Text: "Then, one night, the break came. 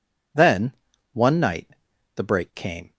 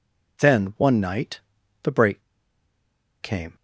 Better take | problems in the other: first | pauses between "break" and "came"; at 2.2 s; 1.0 s long

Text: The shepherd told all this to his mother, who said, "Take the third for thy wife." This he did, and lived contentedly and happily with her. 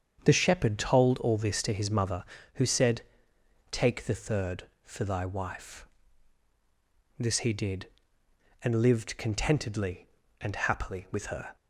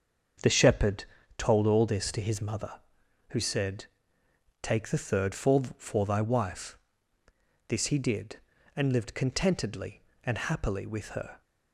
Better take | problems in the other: first | starts louder than the rest; until 1.7 s; 7 dB; strong in the first // pauses between "shepherd" and "told"; slight; at 1.0 s; 0.34 s long // says "for" twice; at 5.7 s

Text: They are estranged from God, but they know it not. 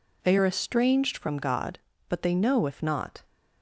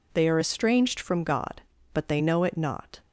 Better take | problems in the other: second | says "if" for "it"; at 2.6 s

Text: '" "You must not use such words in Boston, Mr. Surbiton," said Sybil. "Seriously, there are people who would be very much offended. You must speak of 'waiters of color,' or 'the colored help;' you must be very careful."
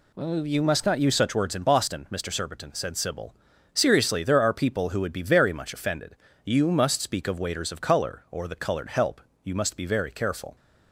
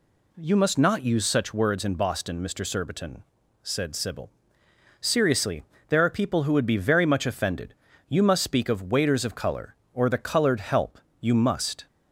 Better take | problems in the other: first | stops before "be very careful"; at 11.8 s

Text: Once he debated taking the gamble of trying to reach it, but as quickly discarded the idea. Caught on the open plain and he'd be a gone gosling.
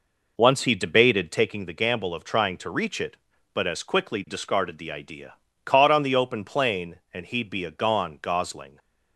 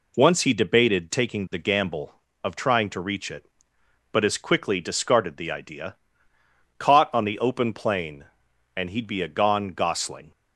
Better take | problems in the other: second | starts louder than the rest; noticeable; until 1.4 s; 4.5 dB

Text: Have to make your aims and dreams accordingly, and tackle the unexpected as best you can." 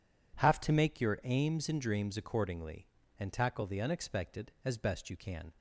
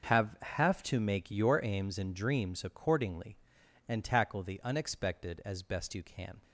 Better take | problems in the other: first | starts louder than the rest; until 1.1 s; 6 dB // says "Have" twice; at 0.4 s

